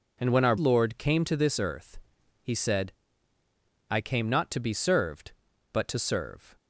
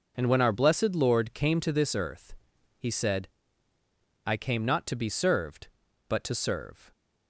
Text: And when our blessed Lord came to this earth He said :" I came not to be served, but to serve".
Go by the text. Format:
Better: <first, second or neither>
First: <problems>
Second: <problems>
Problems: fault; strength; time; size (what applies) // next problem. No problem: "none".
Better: second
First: skips "blessed"; at 0.5 s // pauses between "earth" and "He"; at 1.9 s; 0.44 s long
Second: pauses between "earth" and "He"; at 2.3 s; 0.44 s long